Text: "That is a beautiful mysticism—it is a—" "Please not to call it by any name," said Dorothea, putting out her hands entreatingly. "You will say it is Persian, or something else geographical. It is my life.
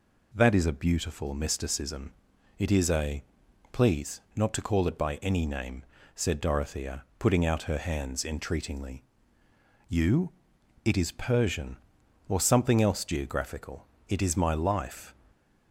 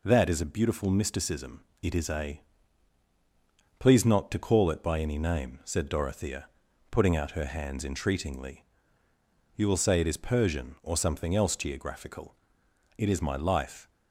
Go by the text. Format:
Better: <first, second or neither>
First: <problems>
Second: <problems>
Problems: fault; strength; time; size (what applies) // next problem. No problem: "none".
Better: second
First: skips "will say"; at 10.5 s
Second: none